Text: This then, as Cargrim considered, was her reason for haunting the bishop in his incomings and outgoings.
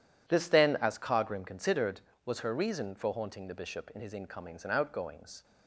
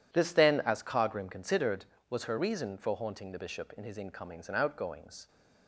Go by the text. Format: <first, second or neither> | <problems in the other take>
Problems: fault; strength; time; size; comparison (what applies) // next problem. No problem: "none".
neither | none